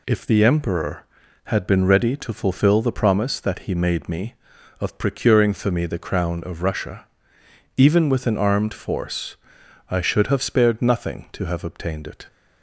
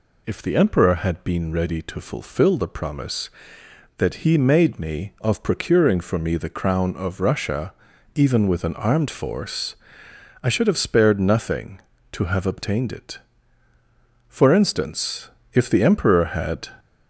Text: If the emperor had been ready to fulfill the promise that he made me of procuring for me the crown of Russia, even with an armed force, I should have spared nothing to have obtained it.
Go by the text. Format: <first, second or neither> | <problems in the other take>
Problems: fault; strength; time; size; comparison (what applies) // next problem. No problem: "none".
first | goes on to say "For instance if the emperor had"; strong; from 14.2 s on; 2.4 s long